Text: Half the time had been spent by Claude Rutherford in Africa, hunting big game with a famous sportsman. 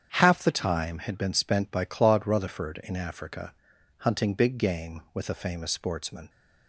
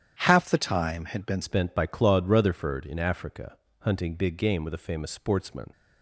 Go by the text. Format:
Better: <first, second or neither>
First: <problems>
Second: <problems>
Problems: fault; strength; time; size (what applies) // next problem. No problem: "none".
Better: first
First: starts louder than the rest; strong; until 1.1 s; 8 dB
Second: starts louder than the rest; strong; until 1.2 s; 10 dB // changes voice at "spent"; from 1.4 s on; 4.3 s long